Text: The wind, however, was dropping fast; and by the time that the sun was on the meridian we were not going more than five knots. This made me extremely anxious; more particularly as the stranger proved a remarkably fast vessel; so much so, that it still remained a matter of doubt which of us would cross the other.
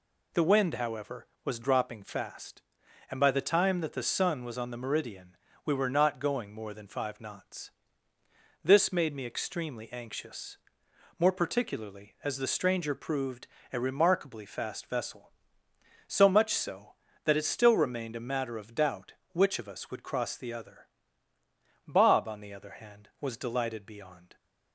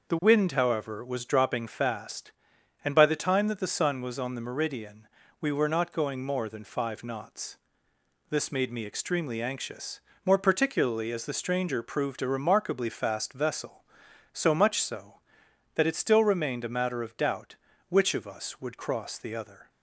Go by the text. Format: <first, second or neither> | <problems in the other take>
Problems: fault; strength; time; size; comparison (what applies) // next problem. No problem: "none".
second | pauses between "meridian" and "we"; slight; at 5.3 s; 0.26 s long; slight in the second // pauses between "proved" and "a"; slight; at 13.4 s; 0.24 s long // goes on to say "Bob on the other hand was delighted beyond"; strong; from 21.8 s on; 2.4 s long